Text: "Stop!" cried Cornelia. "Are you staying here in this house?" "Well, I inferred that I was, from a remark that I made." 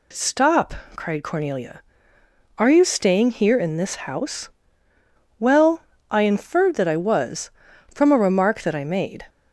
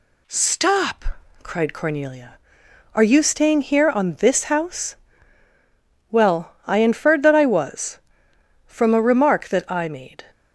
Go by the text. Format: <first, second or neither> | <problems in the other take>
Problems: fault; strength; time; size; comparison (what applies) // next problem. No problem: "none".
first | says "on" for "in"; at 3.9 s